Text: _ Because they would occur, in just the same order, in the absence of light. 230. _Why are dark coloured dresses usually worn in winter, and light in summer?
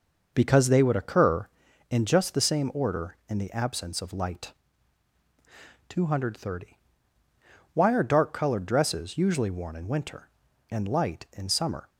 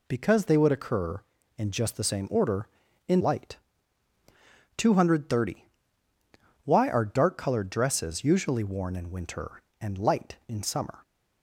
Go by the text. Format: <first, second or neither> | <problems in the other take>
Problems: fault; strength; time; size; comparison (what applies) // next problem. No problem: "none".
first | skips "the absence of"; at 3.2 s